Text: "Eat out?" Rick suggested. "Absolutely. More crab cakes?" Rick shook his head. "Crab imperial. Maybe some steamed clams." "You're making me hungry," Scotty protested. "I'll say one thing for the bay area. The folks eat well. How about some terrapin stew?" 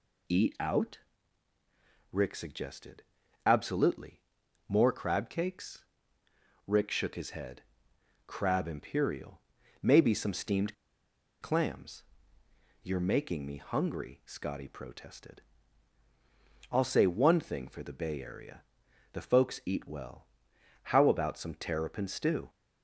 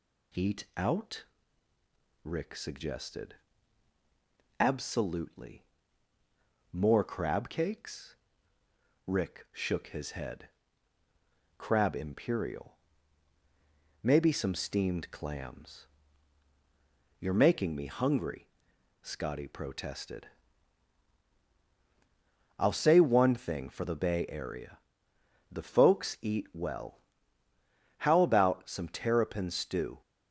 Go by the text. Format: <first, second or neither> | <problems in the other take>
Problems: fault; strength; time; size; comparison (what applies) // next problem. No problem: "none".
second | pauses between "steamed" and "clams"; noticeable; at 10.7 s; 0.66 s long